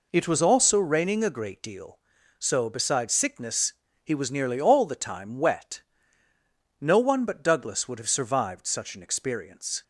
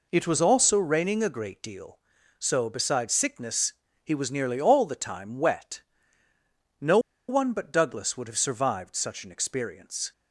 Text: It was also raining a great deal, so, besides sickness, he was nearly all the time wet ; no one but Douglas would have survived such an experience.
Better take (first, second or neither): first